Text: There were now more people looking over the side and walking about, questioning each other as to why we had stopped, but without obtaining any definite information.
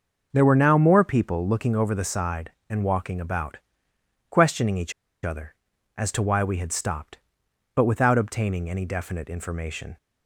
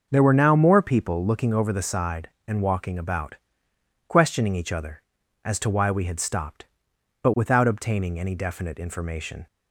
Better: second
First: starts louder than the rest; noticeable; until 1.3 s; 6 dB // pauses between "each" and "other"; slight; at 4.9 s; 0.32 s long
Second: starts louder than the rest; noticeable; until 1.1 s; 6 dB

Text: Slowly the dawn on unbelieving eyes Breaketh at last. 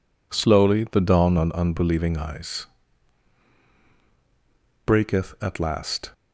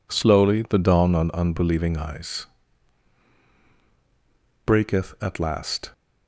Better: neither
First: pauses between "eyes" and "Breaketh"; strong; at 2.6 s; 2.1 s long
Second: pauses between "eyes" and "Breaketh"; strong; at 2.4 s; 2.1 s long

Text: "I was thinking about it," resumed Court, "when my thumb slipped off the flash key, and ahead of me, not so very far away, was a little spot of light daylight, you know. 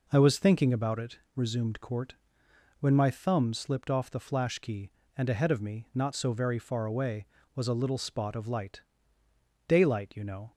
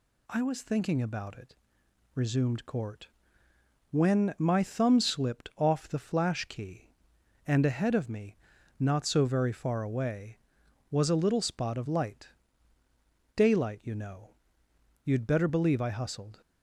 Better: first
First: pauses between "light" and "daylight"; noticeable; at 8.8 s; 0.84 s long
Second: pauses between "light" and "daylight"; at 12.2 s; 1.0 s long // goes on to say "You'd better believe I hustled"; from 15.0 s on; 1.3 s long

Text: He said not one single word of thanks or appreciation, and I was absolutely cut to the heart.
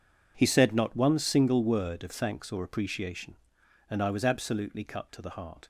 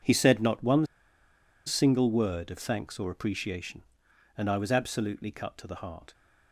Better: first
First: none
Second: pauses between "one" and "single"; noticeable; at 0.8 s; 0.81 s long

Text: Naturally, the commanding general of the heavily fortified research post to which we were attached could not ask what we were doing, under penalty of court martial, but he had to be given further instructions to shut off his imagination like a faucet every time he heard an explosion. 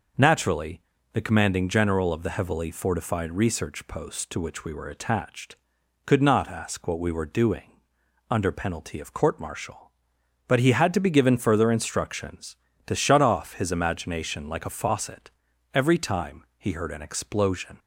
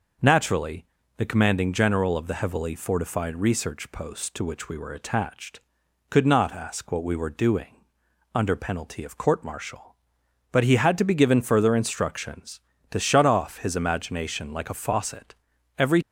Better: first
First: pauses between "faucet" and "every"; at 15.3 s; 0.42 s long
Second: pauses between "faucet" and "every"; at 15.3 s; 0.42 s long // stops before "time he heard an explosion"; at 16.0 s

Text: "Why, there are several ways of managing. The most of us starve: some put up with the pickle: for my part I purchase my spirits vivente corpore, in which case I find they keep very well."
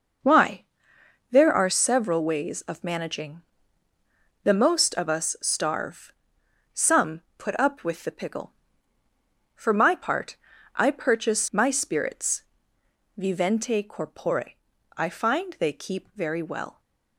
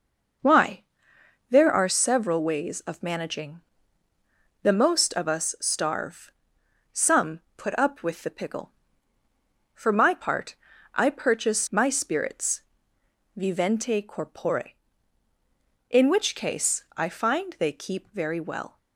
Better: second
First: pauses between "some" and "put"; slight; at 7.2 s; 0.16 s long // pauses between "part" and "I"; at 10.3 s; 0.38 s long // pauses between "spirits" and "vivente"; noticeable; at 12.4 s; 0.74 s long // skips "in which case"; at 14.7 s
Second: pauses between "some" and "put"; slight; at 7.4 s; 0.16 s long // pauses between "part" and "I"; at 10.5 s; 0.38 s long // pauses between "spirits" and "vivente"; noticeable; at 12.6 s; 0.74 s long

